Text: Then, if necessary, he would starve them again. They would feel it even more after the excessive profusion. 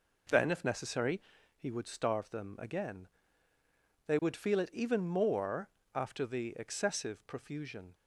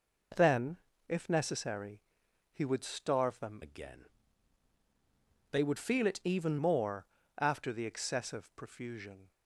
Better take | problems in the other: first | changes voice from "again" to "even"; from 3.6 to 6.5 s; 2.9 s long // pauses between "more" and "after"; slight; at 7.0 s; 0.32 s long; slight in the first

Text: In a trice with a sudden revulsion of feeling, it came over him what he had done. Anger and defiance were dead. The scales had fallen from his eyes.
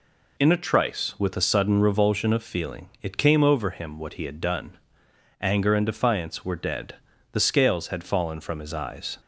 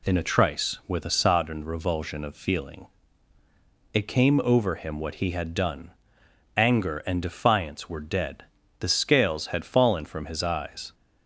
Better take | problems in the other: first | says "sodden" for "sudden"; at 1.0 s

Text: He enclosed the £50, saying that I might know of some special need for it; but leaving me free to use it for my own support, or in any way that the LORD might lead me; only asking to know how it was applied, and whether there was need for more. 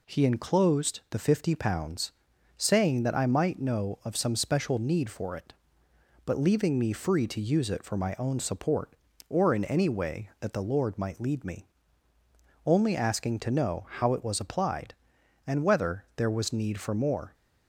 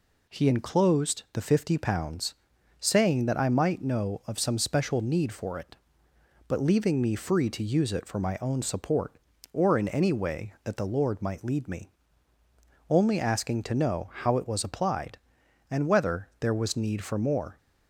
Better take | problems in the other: neither | none

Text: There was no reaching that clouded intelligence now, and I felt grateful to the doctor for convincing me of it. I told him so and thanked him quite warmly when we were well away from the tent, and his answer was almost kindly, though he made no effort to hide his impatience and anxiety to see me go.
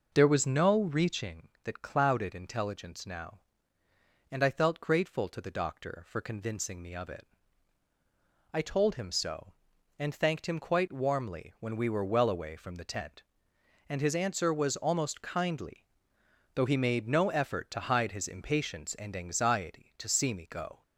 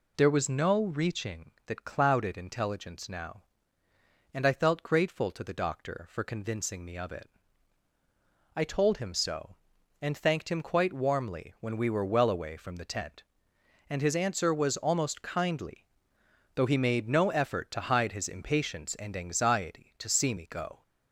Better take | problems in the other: second | starts louder than the rest; noticeable; until 1.3 s; 5.5 dB

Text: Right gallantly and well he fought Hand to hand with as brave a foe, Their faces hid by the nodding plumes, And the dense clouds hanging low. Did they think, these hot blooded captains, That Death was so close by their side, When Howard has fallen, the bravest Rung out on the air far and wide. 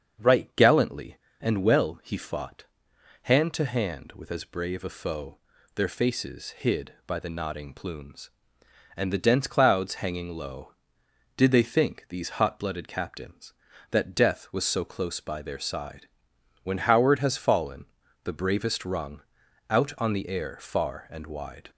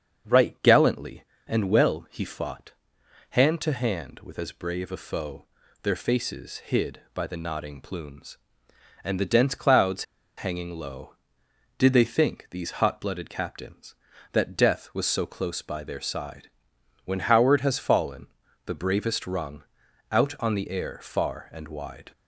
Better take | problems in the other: first | starts louder than the rest; until 1.5 s; 7 dB; also in the first // pauses between "fought" and "Hand"; noticeable; at 2.7 s; 0.58 s long; noticeable in the first // pauses between "clouds" and "hanging"; slight; at 10.0 s; 0.32 s long // pauses between "Rung" and "out"; noticeable; at 19.6 s; 0.48 s long; noticeable in the first

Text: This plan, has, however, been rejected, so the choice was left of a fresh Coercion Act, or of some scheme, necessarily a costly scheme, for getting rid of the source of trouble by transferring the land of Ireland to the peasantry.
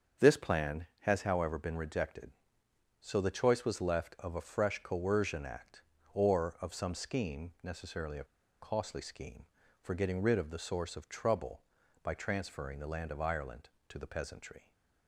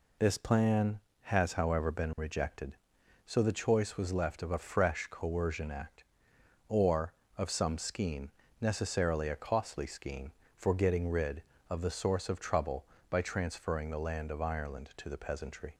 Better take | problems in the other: second | starts louder than the rest; until 1.3 s; 7 dB // pauses between "a" and "costly"; at 8.2 s; 0.36 s long

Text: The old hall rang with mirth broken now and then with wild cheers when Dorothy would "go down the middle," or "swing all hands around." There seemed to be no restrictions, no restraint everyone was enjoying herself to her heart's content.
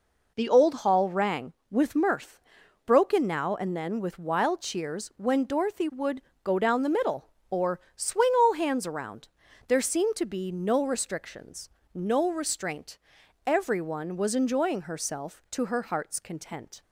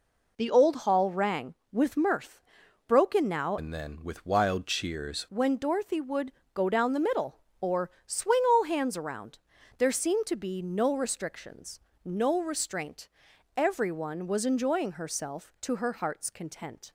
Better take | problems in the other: first | pauses between "mirth" and "broken"; noticeable; at 2.4 s; 0.46 s long; noticeable in the first // changes voice from "and" to "cheers"; from 3.5 to 5.2 s; 1.7 s long // pauses between "would" and "go"; slight; at 6.3 s; 0.22 s long; slight in the first // pauses between "or" and "swing"; slight; at 7.8 s; 0.16 s long; slight in the first // pauses between "restraint" and "everyone"; noticeable; at 13.0 s; 0.48 s long; noticeable in the first

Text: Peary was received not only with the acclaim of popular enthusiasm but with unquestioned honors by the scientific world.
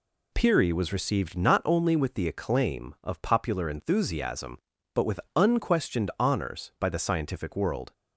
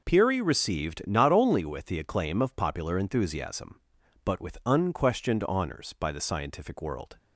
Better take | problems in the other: first | skips "was"; at 0.4 s

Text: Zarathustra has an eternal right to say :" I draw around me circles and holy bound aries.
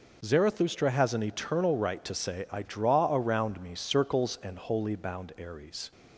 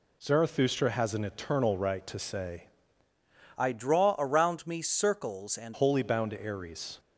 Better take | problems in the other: first | changes voice from "I" to "and"; from 3.5 to 5.7 s; 2.2 s long

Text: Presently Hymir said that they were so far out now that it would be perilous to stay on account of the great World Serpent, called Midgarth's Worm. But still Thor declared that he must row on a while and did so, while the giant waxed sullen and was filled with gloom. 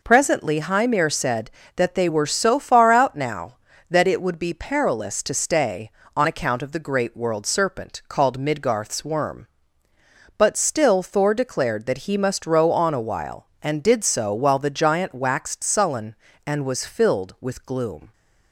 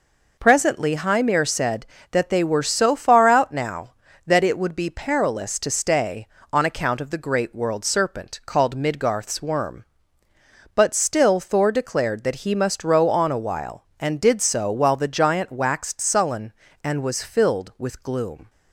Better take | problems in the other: neither | none

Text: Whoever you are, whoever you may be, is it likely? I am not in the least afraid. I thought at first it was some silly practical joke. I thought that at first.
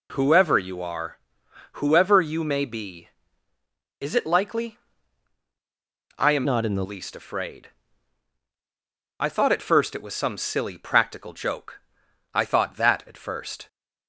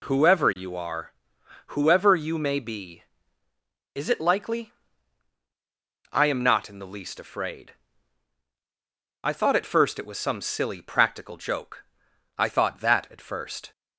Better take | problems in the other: second | changes voice from "not" to "the"; from 6.4 to 6.8 s; 0.4 s long

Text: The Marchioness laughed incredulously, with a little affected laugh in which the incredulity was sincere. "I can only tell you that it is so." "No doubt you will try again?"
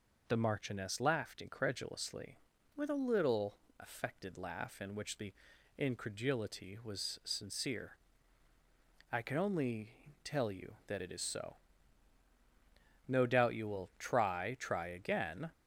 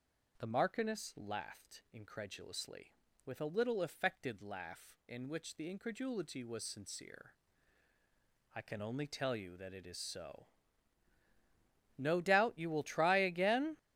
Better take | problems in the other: second | pauses between "little" and "affected"; slight; at 3.5 s; 0.22 s long // pauses between "the" and "incredulity"; at 5.3 s; 0.44 s long // pauses between "only" and "tell"; slight; at 9.9 s; 0.32 s long // says "try" twice; at 14.5 s

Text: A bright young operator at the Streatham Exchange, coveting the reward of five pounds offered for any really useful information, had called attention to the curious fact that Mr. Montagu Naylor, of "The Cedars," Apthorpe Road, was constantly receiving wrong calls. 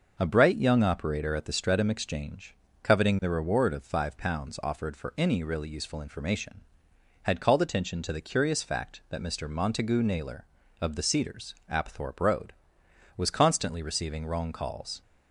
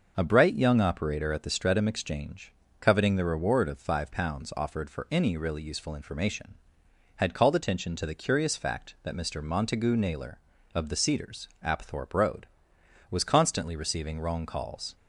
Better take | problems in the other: neither | none

